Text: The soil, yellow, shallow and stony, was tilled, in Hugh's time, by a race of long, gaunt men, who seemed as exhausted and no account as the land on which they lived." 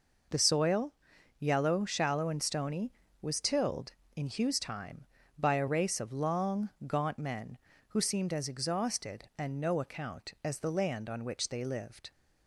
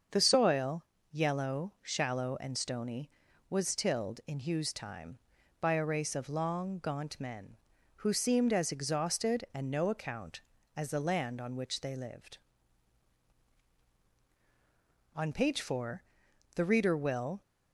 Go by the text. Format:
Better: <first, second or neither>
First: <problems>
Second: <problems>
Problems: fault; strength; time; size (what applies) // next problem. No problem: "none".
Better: first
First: none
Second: starts louder than the rest; until 1.3 s; 7 dB // goes on to say "On page four the reader will"; strong; from 15.1 s on; 2.2 s long